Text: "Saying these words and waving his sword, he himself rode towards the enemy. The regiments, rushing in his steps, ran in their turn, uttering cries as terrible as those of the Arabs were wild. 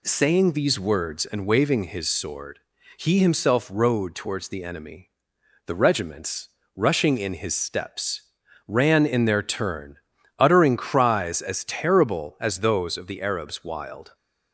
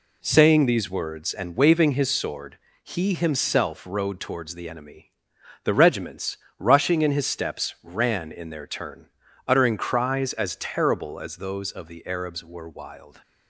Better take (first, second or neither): second